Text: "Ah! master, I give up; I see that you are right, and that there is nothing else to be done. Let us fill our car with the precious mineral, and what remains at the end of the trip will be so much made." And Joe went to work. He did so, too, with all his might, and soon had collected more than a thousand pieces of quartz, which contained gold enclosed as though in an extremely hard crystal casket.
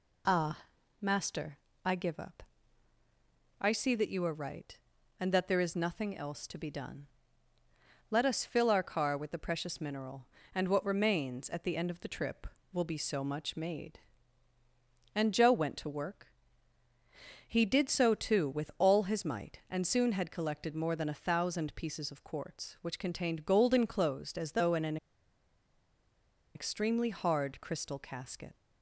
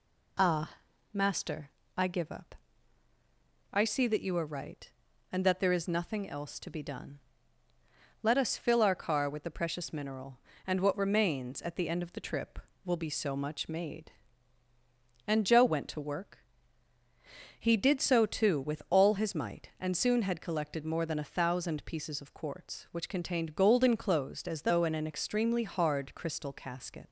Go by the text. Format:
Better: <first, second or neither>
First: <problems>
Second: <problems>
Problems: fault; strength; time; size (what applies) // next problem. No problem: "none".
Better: second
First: pauses between "an" and "extremely"; strong; at 24.9 s; 1.5 s long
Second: none